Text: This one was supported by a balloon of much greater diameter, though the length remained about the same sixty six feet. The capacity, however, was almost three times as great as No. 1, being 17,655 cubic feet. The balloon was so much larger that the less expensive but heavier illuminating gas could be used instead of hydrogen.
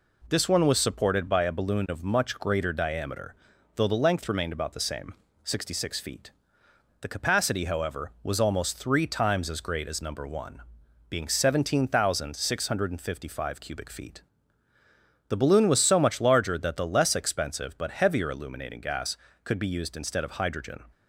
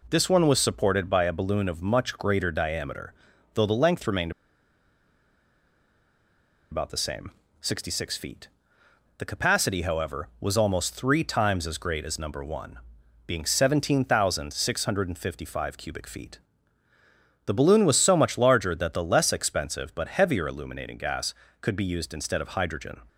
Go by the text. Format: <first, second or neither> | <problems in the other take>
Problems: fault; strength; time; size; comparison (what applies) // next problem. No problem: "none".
first | pauses between "remained" and "about"; strong; at 4.3 s; 2.4 s long // pauses between "same" and "sixty"; slight; at 7.3 s; 0.28 s long; slight in the first